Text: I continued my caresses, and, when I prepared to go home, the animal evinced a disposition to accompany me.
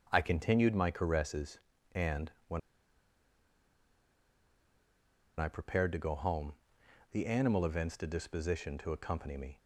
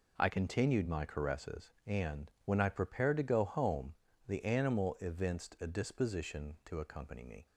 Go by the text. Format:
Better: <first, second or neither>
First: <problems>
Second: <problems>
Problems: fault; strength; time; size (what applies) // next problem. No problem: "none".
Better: second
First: starts louder than the rest; until 1.1 s; 7 dB // pauses between "when" and "I"; strong; at 2.5 s; 2.7 s long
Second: none